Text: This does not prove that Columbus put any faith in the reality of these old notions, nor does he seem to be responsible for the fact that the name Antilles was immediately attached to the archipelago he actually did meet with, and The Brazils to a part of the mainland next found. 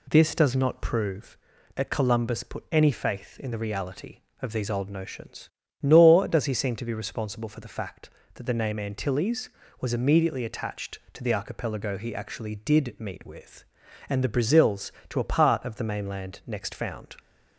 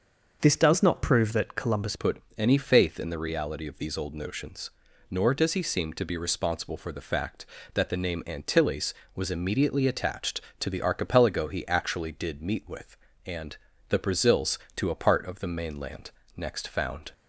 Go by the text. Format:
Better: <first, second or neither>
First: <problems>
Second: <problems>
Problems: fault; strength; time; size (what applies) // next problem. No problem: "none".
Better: first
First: none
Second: starts louder than the rest; until 1.4 s; 6.5 dB // changes voice at "put"; from 1.9 s on; 15.2 s long // pauses between "put" and "any"; slight; at 2.2 s; 0.16 s long // pauses between "and" and "The"; slight; at 13.5 s; 0.32 s long // pauses between "mainland" and "next"; slight; at 16.1 s; 0.26 s long